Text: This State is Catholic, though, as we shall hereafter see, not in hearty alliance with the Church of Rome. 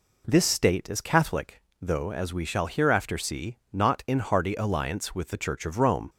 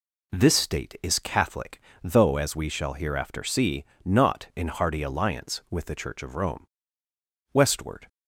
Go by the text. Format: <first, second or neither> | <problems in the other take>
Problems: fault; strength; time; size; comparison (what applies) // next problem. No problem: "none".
first | goes on to say "Westward"; from 7.5 s on; 0.54 s long